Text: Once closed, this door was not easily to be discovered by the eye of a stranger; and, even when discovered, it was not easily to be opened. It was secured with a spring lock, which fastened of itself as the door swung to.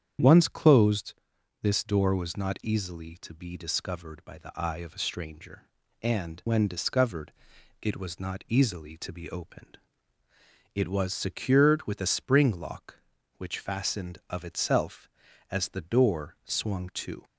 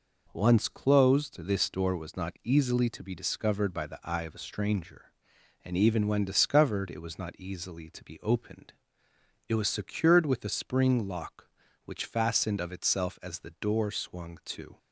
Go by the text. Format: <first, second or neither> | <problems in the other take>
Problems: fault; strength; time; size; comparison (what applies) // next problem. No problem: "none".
second | starts louder than the rest; strong; until 1.6 s; 9 dB // skips "even"; at 6.4 s